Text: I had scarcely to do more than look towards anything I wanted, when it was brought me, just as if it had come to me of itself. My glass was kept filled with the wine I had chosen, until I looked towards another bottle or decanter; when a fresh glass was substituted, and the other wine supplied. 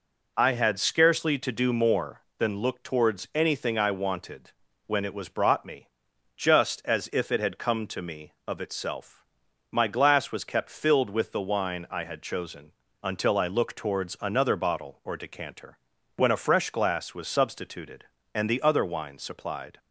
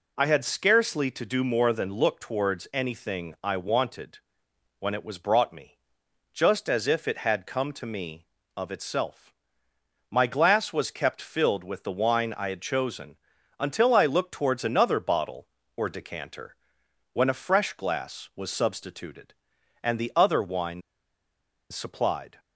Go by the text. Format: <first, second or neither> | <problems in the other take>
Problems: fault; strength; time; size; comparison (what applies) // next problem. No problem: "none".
first | pauses between "wine" and "supplied"; noticeable; at 20.8 s; 0.89 s long